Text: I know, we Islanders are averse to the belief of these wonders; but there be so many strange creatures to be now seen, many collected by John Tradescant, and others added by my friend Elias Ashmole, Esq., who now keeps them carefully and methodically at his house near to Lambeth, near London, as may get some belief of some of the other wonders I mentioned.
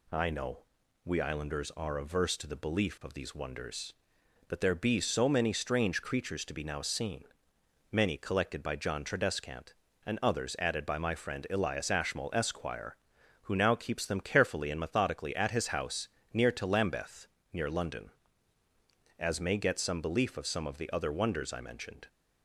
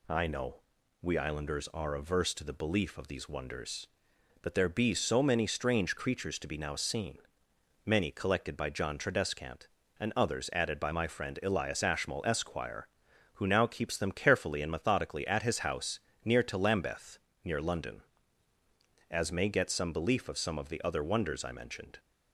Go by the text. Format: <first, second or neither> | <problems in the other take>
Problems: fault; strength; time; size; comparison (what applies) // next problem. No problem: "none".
neither | pauses between "house" and "near"; slight; the same in both